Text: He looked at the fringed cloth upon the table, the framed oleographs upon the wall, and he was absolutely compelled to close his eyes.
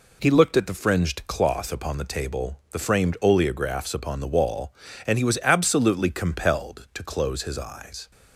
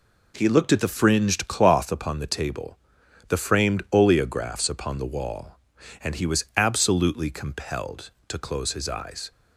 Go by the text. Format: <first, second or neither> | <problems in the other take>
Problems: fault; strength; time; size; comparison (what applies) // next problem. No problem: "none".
neither | none